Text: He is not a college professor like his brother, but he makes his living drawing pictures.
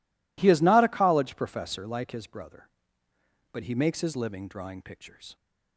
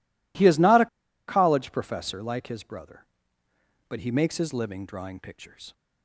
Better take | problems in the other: first | pauses between "a" and "college"; at 0.8 s; 0.41 s long

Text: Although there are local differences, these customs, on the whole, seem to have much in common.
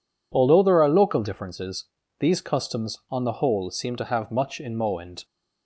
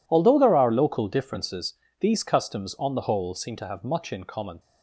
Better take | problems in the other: second | says "moend" for "common"; at 4.7 s

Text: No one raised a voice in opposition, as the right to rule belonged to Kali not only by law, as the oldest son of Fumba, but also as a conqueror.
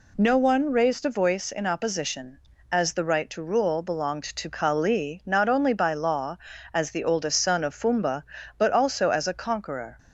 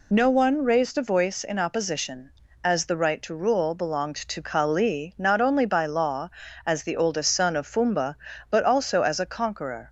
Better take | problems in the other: first | loses the start of "No"; at 0.1 s; 25 ms

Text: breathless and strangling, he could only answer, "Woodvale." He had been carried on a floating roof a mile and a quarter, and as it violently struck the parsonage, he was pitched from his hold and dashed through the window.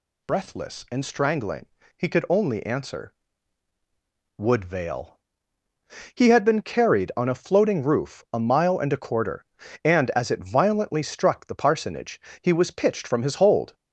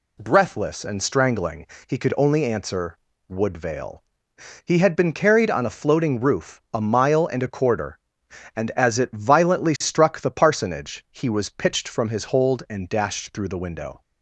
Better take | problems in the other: second | stops before "and dashed through the window"; at 13.7 s

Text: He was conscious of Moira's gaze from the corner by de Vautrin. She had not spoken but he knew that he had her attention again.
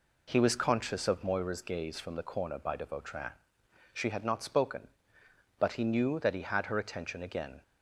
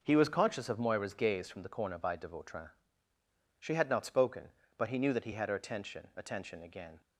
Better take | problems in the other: first | says "attention" twice; at 6.1 s

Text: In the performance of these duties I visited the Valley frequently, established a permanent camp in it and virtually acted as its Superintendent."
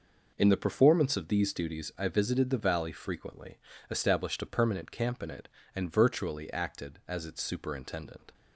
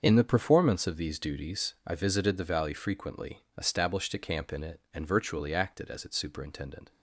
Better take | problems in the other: first | starts louder than the rest; until 1.0 s; 7 dB // skips "permanent"; at 4.1 s

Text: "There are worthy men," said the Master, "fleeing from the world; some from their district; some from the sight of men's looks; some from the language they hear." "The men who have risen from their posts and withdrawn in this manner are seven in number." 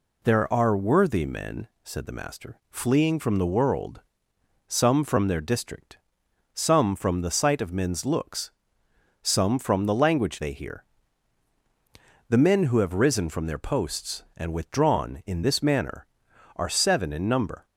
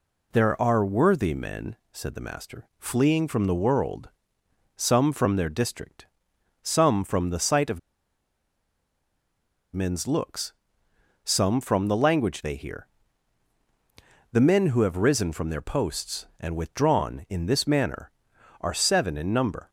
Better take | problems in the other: first | pauses between "of" and "men's"; strong; at 7.7 s; 1.9 s long

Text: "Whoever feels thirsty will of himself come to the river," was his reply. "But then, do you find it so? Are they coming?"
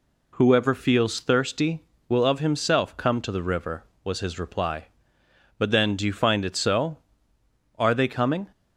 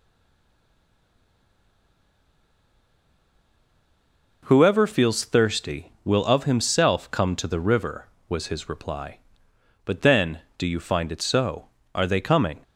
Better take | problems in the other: first | stays silent before the first word; strong; until 4.4 s; 4.4 s long

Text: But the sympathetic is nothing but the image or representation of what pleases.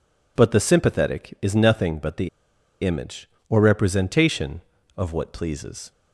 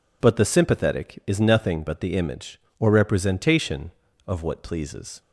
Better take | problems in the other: second | pauses between "the" and "image"; noticeable; at 2.2 s; 0.53 s long

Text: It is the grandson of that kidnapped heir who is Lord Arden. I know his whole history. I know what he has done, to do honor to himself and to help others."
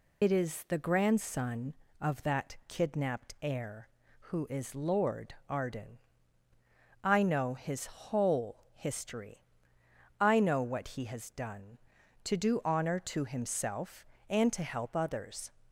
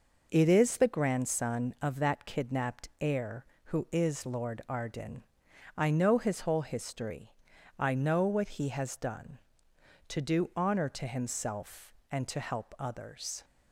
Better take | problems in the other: second | loses the start of "It"; at 0.2 s; 85 ms // pauses between "Lord" and "Arden"; slight; at 5.3 s; 0.16 s long

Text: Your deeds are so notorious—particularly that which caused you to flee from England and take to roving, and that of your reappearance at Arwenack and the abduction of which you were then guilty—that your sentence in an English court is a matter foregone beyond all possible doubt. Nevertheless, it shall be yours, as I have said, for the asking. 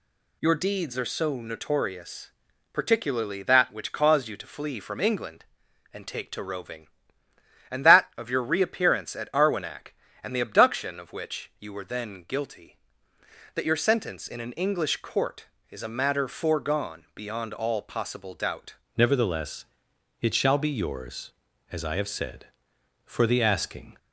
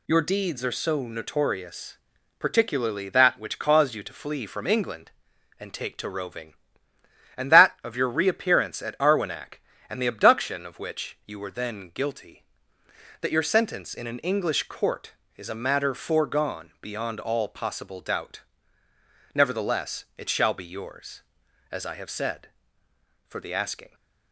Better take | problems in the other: second | changes voice at "Nevertheless"; from 18.9 s on; 5.0 s long

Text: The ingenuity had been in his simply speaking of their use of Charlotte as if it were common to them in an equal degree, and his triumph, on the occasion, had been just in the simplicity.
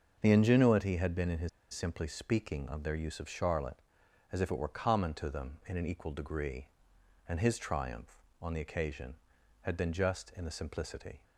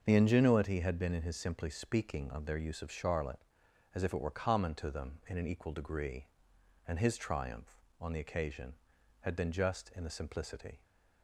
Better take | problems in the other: second | starts louder than the rest; until 1.2 s; 6.5 dB; also in the second // pauses between "his" and "simply"; slight; at 1.4 s; 0.23 s long

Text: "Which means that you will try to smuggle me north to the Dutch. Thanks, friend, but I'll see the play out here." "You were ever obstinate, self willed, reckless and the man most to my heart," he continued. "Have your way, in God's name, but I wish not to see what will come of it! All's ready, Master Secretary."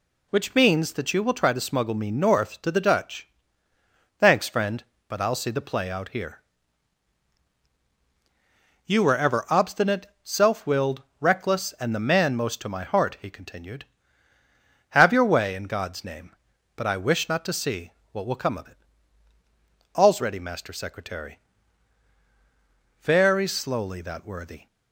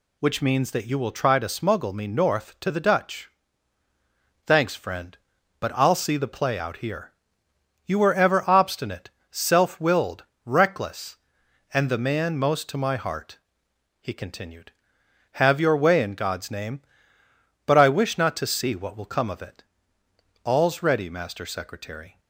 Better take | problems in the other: second | pauses between "see" and "what"; slight; at 17.9 s; 0.22 s long // goes on to say "Very slowly that worthy"; from 23.0 s on; 1.6 s long

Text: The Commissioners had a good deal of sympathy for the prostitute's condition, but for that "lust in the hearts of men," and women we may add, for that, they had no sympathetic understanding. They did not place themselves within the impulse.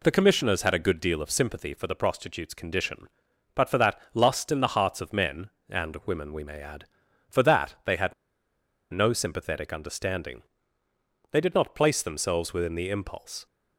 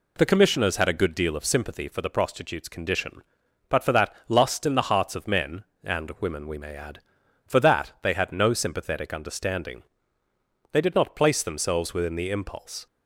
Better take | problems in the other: second | pauses between "had" and "no"; noticeable; at 8.1 s; 0.77 s long

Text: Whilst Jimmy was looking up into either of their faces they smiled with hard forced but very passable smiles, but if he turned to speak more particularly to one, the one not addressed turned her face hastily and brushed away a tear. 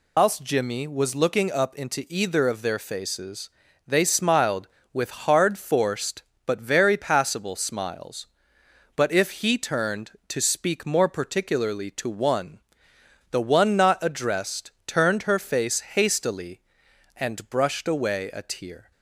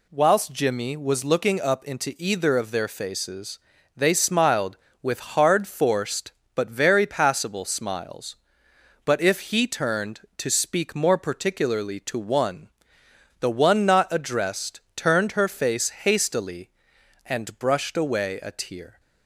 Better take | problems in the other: second | loses the start of "Whilst"; at 0.1 s; 160 ms // pauses between "faces" and "they"; slight; at 3.4 s; 0.36 s long; slight in the second // pauses between "addressed" and "turned"; slight; at 14.7 s; 0.16 s long; slight in the second

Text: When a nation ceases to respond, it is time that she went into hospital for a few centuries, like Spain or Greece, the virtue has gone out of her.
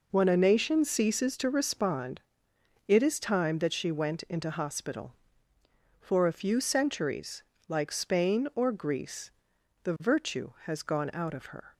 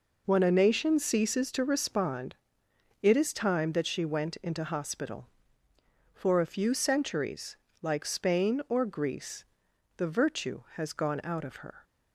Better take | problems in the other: neither | none

